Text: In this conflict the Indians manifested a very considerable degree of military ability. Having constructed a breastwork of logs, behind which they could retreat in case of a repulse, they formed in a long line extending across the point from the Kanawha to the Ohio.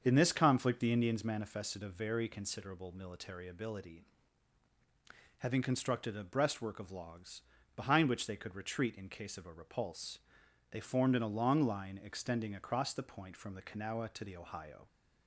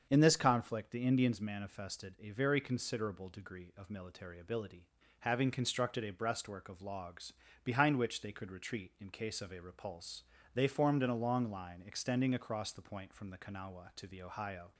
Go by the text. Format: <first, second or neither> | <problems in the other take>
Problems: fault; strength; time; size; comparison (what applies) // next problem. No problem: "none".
second | starts louder than the rest; until 1.0 s; 7 dB; also in the second // skips "degree of"; at 2.9 s